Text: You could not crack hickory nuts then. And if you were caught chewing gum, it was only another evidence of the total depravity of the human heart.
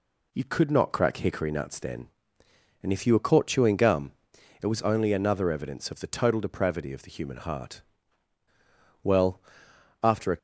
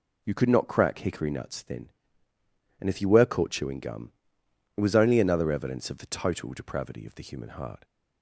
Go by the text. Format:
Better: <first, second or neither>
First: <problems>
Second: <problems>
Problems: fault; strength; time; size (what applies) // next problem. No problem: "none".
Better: second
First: goes on to say "Well after a"; from 9.0 s on; 1.3 s long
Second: none